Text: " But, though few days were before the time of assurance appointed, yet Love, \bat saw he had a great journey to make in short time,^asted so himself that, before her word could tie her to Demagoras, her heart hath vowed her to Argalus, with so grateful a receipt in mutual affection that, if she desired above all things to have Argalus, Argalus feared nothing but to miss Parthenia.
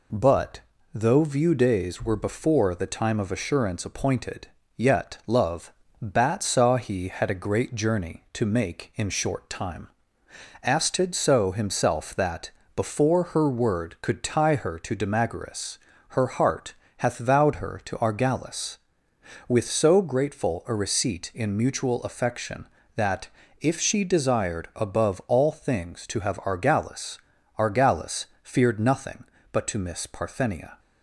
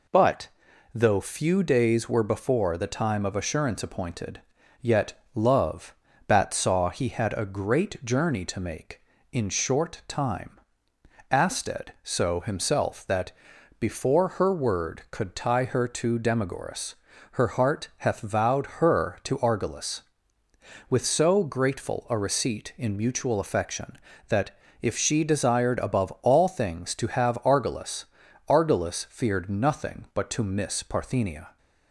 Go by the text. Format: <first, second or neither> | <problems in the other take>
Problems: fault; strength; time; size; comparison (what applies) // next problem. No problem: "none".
second | says "view" for "few"; at 1.2 s // pauses between "heart" and "hath"; slight; at 16.7 s; 0.24 s long // pauses between "Argalus" and "feared"; slight; at 28.2 s; 0.18 s long